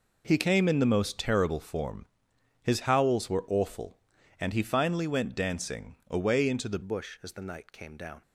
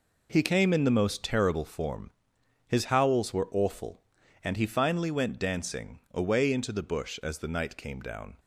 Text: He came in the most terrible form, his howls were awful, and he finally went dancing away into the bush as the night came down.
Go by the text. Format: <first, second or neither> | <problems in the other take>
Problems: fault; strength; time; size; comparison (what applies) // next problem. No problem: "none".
second | pauses between "dancing" and "away"; slight; at 5.9 s; 0.16 s long; slight in the second // changes voice at "bush"; from 6.8 s on; 1.4 s long